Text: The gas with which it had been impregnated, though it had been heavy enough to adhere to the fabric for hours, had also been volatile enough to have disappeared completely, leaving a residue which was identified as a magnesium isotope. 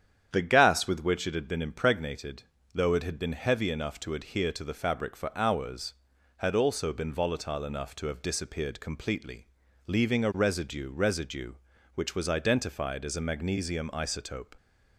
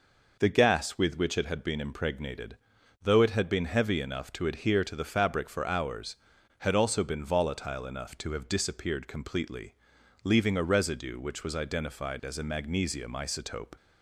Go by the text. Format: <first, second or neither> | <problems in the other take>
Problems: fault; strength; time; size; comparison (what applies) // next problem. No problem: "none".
second | starts louder than the rest; strong; until 1.3 s; 9 dB // says "residue" twice; at 10.9 s